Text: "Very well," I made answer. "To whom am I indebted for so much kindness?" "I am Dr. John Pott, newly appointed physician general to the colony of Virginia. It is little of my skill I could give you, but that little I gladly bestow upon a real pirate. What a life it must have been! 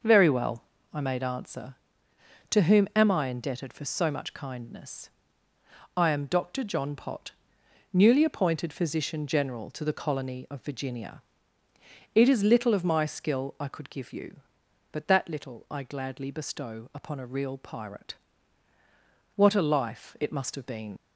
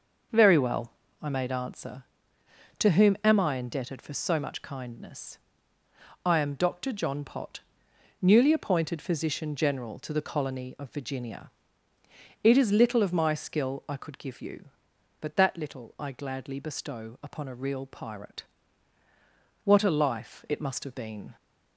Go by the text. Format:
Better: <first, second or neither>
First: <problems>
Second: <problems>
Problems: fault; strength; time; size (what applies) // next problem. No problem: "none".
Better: second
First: leaves "been" unfinished; at 20.9 s; 105 ms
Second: none